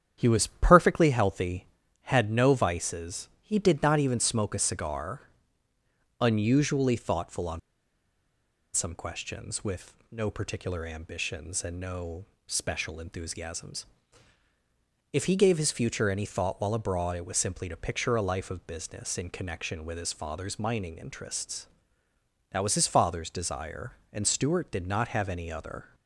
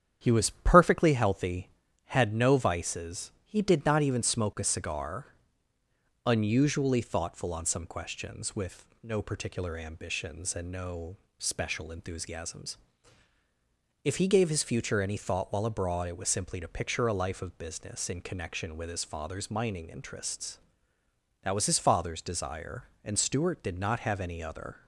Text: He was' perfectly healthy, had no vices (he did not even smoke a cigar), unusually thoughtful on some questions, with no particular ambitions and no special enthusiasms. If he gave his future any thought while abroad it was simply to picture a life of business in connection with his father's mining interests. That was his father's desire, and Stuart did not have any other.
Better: second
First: starts louder than the rest; strong; until 1.1 s; 9 dB // pauses between "on" and "some"; at 7.5 s; 1.1 s long // pauses between "with" and "no"; slight; at 9.9 s; 0.16 s long // pauses between "no" and "special"; slight; at 12.2 s; 0.20 s long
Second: starts louder than the rest; strong; until 1.2 s; 9 dB // pauses between "with" and "no"; slight; at 8.8 s; 0.16 s long // pauses between "no" and "special"; slight; at 11.1 s; 0.20 s long

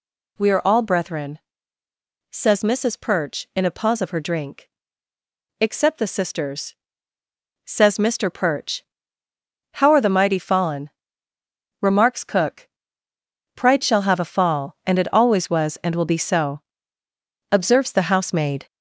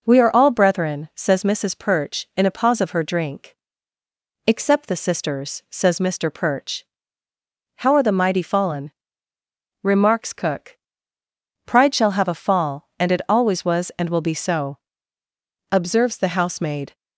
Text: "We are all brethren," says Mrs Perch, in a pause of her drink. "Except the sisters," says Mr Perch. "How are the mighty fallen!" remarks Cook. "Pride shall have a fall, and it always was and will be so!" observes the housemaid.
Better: second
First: gets louder; noticeable; throughout; 5 dB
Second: none

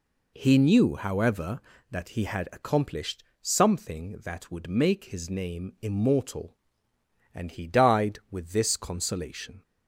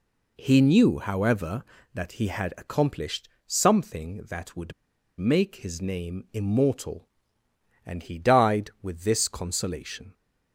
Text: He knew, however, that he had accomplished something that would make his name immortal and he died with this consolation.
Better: first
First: pauses between "accomplished" and "something"; slight; at 3.2 s; 0.18 s long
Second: pauses between "accomplished" and "something"; slight; at 3.2 s; 0.18 s long // pauses between "would" and "make"; noticeable; at 4.7 s; 0.46 s long

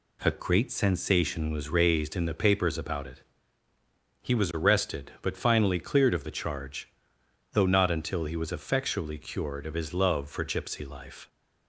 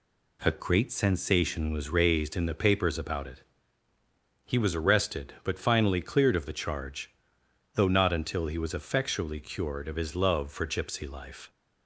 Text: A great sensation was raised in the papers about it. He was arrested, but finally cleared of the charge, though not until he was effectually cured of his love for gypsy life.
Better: neither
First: none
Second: none

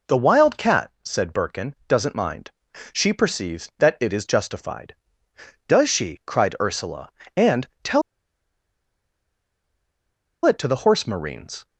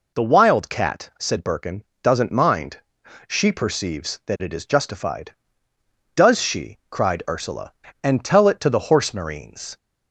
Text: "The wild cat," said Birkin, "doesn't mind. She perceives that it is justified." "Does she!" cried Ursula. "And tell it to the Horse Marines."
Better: second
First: pauses between "And" and "tell"; slight; at 7.6 s; 0.16 s long // pauses between "tell" and "it"; strong; at 8.0 s; 2.4 s long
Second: none

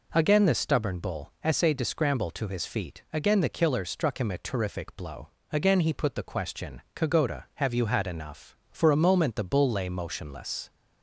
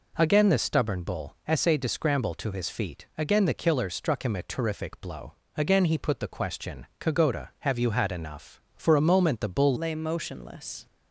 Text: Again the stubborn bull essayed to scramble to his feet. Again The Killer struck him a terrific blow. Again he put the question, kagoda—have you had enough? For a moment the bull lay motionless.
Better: first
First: none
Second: changes voice at "lay"; from 9.7 s on; 1.1 s long

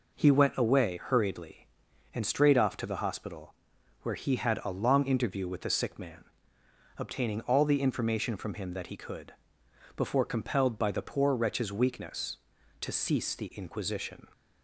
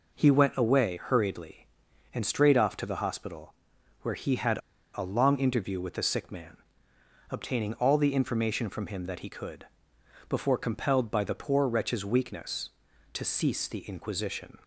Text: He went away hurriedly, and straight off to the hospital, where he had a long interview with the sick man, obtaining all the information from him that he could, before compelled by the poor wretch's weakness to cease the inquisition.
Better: first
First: none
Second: pauses between "had" and "a"; slight; at 4.5 s; 0.35 s long

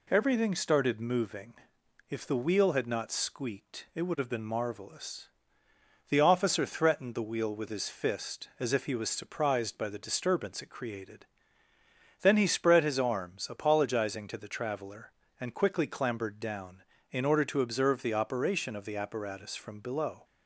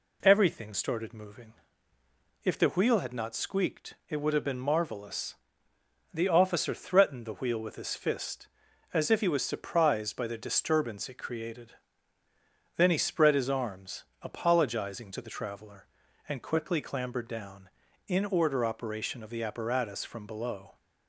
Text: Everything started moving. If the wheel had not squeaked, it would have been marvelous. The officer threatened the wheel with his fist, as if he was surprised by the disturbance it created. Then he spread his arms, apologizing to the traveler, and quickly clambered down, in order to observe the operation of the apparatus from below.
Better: first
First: none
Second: skips "to observe the"; at 18.6 s

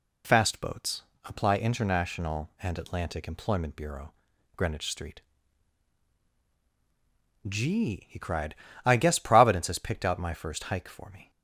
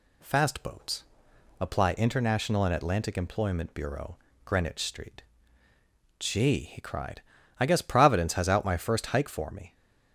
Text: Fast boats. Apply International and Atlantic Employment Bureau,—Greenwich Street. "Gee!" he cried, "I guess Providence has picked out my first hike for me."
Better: first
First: none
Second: skips "picked"; at 8.4 s

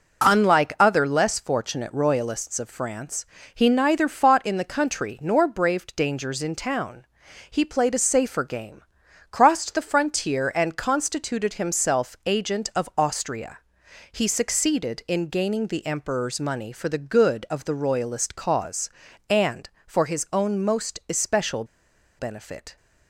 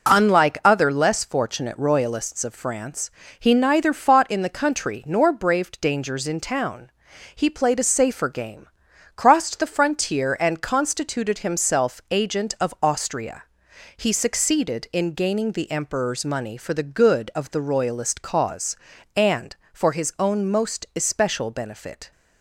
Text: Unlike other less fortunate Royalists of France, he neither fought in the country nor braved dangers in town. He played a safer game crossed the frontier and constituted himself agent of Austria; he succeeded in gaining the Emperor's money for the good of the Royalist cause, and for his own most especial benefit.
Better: second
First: pauses between "game" and "crossed"; noticeable; at 8.8 s; 0.50 s long // pauses between "especial" and "benefit"; noticeable; at 21.6 s; 0.54 s long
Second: pauses between "game" and "crossed"; noticeable; at 8.6 s; 0.50 s long

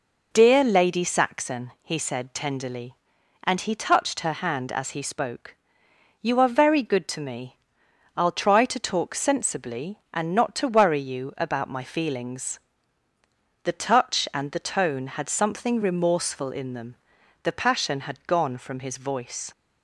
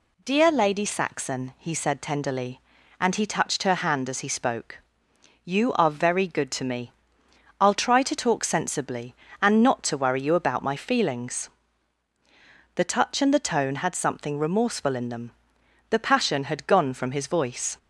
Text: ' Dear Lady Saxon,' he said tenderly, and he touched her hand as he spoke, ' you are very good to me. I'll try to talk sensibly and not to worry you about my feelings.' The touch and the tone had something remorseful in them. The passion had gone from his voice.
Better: neither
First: none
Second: none

